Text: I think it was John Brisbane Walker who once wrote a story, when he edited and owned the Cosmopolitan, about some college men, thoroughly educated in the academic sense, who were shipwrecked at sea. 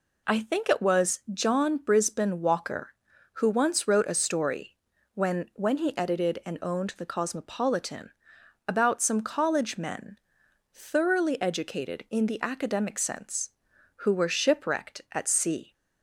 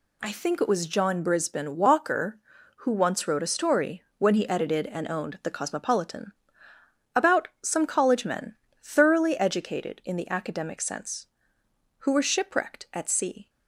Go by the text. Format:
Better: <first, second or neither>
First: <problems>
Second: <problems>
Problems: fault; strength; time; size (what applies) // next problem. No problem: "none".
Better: second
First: says "when" twice; at 5.5 s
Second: none